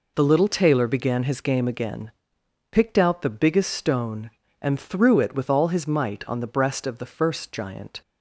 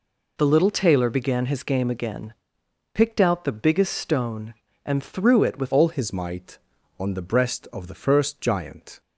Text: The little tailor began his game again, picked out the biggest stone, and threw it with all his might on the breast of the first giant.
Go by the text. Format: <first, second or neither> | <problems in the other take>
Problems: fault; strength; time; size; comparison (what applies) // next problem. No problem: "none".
first | changes voice at "all"; from 5.7 s on; 3.3 s long